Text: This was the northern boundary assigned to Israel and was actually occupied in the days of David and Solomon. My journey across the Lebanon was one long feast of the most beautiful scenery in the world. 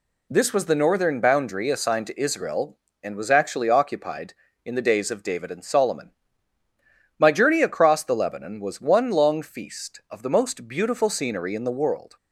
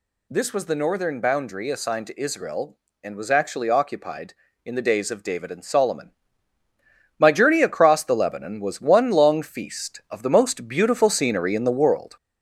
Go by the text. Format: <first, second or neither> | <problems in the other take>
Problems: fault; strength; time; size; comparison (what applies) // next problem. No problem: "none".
first | gets louder; slight; throughout; 3.5 dB